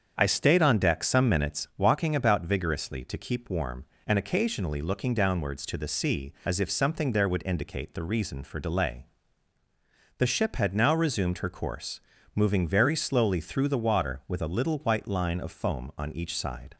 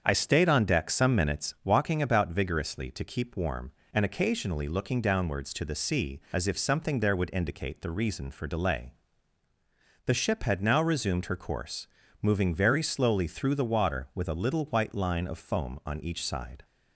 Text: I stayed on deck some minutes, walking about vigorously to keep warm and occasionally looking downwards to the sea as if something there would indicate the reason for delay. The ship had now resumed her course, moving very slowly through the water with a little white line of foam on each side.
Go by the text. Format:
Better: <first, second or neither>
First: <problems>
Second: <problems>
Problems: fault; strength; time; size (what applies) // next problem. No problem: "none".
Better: neither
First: starts louder than the rest; strong; until 1.1 s; 7.5 dB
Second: starts louder than the rest; strong; until 1.0 s; 7.5 dB